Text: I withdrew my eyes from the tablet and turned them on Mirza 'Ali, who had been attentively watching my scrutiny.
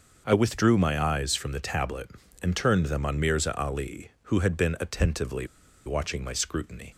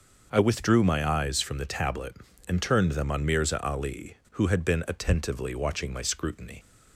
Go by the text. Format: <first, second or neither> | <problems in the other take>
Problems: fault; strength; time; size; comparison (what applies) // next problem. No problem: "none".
second | pauses between "attentively" and "watching"; at 5.4 s; 0.39 s long